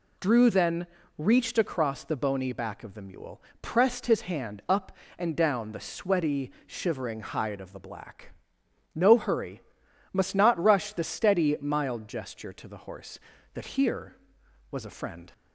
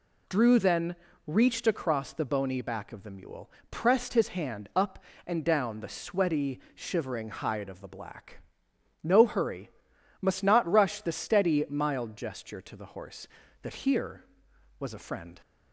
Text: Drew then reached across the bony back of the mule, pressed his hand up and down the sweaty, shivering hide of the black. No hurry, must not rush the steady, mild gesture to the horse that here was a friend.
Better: neither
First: pauses between "then" and "reached"; slight; at 0.8 s; 0.32 s long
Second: pauses between "then" and "reached"; slight; at 0.9 s; 0.32 s long

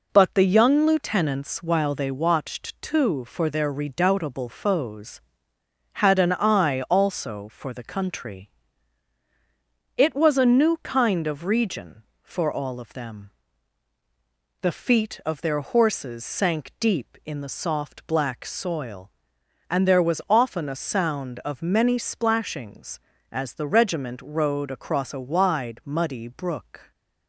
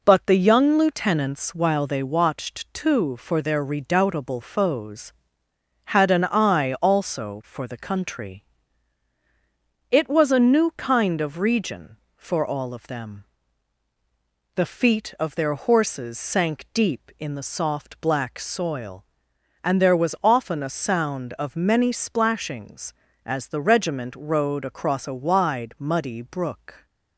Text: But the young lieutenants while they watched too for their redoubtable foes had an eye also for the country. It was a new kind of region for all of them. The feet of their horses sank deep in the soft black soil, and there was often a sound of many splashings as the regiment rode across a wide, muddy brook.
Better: neither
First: none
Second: none

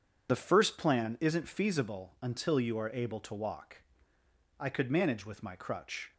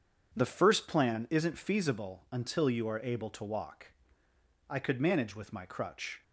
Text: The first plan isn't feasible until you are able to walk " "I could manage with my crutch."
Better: second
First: loses the start of "The"; at 0.2 s; 70 ms // starts louder than the rest; strong; until 1.3 s; 8 dB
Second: starts louder than the rest; strong; until 1.3 s; 8 dB

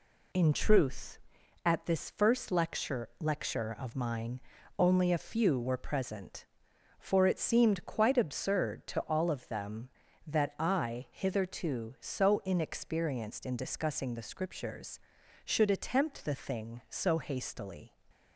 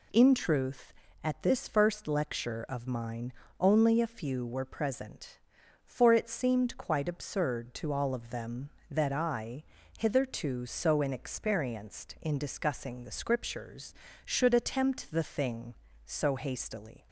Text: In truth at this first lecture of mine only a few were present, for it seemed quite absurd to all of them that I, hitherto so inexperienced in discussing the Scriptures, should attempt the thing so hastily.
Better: second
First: says "lecture" twice; at 3.1 s // pauses between "mine" and "only"; at 4.3 s; 0.38 s long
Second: pauses between "mine" and "only"; slight; at 3.3 s; 0.28 s long

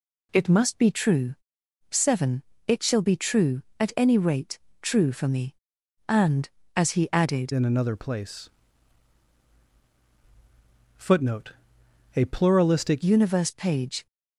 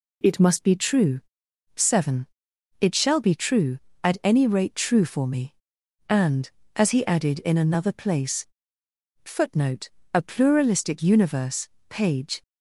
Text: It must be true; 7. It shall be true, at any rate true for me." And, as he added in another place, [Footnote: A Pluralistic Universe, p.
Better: second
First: pauses between "rate" and "true"; slight; at 4.5 s; 0.24 s long // changes voice from "in" to "Pluralistic"; from 7.5 to 13.0 s; 5.5 s long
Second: none

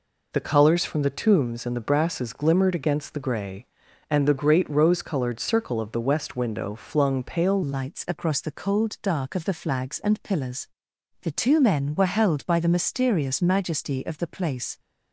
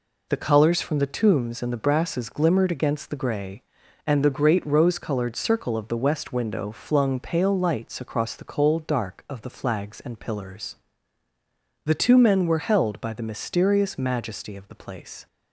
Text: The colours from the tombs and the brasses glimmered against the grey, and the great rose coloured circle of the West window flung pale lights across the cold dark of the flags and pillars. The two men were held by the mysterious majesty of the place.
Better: second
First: changes voice at "lights"; from 7.6 s on; 7.1 s long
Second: none

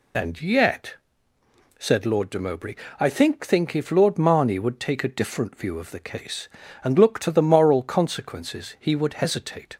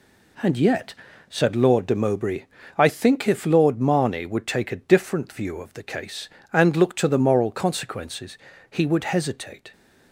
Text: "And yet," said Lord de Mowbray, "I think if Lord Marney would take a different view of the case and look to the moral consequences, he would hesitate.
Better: second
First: says "think" twice; at 3.4 s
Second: none

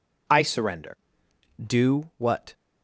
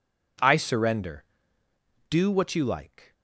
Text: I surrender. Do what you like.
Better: second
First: stops before "you like"; at 2.5 s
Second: none

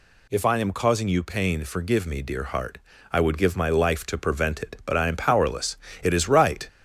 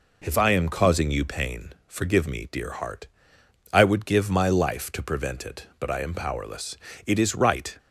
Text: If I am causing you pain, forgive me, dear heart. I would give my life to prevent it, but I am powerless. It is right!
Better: second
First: gets louder; slight; throughout; 2.5 dB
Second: none

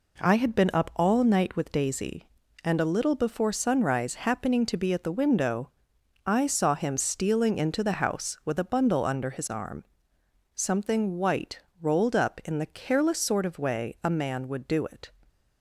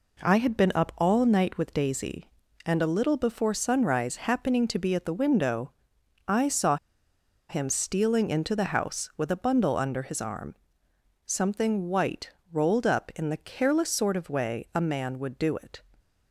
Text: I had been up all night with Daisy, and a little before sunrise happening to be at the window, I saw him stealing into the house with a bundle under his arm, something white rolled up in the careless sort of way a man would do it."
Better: first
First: pauses between "white" and "rolled"; slight; at 11.5 s; 0.20 s long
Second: pauses between "saw" and "him"; noticeable; at 6.7 s; 0.73 s long // pauses between "white" and "rolled"; slight; at 12.3 s; 0.20 s long

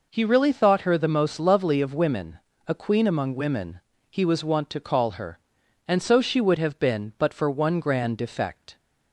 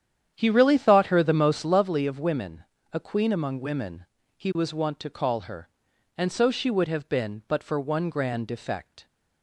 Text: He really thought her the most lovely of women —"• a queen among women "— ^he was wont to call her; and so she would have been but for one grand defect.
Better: first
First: none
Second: starts louder than the rest; strong; until 1.9 s; 9.5 dB

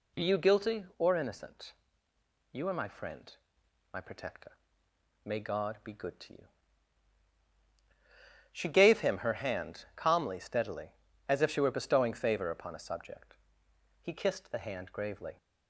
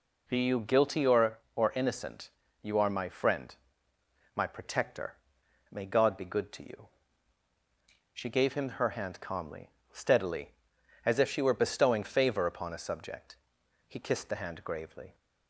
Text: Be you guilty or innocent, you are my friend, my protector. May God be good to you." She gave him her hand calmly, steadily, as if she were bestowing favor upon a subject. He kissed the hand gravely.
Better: first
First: none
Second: says "or" twice; at 1.5 s

